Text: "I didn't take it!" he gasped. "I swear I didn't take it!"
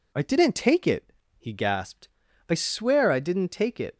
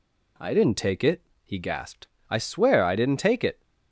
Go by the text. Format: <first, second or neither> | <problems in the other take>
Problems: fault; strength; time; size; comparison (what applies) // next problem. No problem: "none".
neither | none